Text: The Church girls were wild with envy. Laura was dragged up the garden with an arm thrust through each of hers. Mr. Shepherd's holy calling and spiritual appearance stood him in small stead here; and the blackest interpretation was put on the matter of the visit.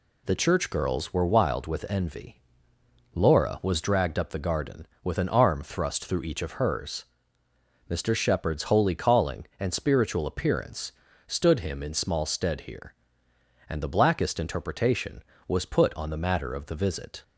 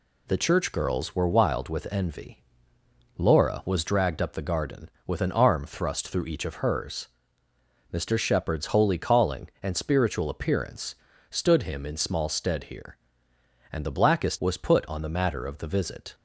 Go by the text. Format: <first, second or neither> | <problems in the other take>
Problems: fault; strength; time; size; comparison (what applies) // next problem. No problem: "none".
first | pauses between "appearance" and "stood"; slight; at 10.9 s; 0.34 s long; slight in the first // skips "interpretation"; at 14.3 s